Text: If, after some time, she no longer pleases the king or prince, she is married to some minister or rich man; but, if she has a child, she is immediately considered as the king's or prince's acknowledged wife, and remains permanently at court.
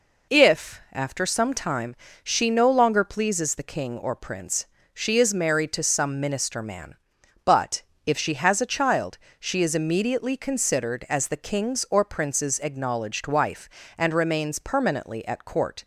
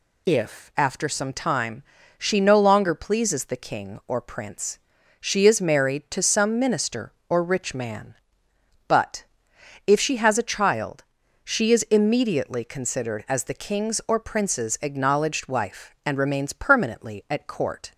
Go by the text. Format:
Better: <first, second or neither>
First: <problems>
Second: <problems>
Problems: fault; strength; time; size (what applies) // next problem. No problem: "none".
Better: second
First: skips "or rich"; at 6.6 s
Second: none